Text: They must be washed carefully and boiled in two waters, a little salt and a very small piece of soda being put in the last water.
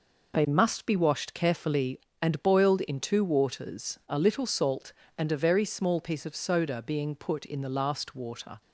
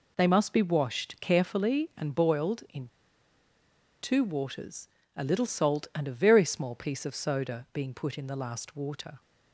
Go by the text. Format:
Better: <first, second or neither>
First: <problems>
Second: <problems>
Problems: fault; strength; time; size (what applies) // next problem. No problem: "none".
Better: first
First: none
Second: pauses between "in" and "two"; at 2.8 s; 1.1 s long